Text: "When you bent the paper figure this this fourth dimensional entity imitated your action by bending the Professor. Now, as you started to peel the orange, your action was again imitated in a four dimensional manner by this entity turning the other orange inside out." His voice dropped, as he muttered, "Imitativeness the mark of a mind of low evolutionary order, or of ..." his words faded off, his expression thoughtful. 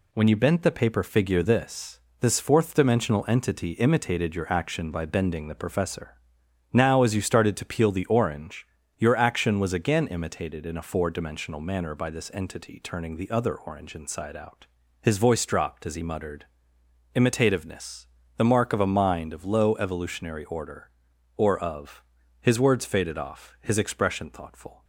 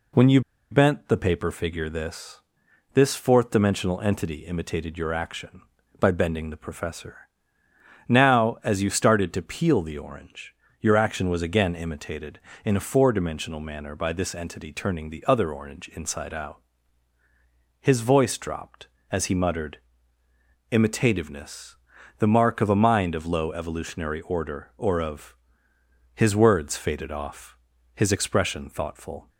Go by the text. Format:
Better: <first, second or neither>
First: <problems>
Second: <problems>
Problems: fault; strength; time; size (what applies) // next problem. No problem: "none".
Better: first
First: pauses between "this" and "this"; slight; at 1.9 s; 0.22 s long // pauses between "Imitativeness" and "the"; slight; at 18.0 s; 0.30 s long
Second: pauses between "you" and "bent"; slight; at 0.4 s; 0.30 s long // pauses between "this" and "this"; noticeable; at 2.4 s; 0.54 s long // pauses between "Imitativeness" and "the"; at 21.7 s; 0.42 s long